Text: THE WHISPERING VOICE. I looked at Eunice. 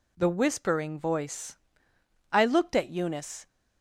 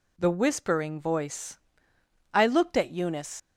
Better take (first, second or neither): first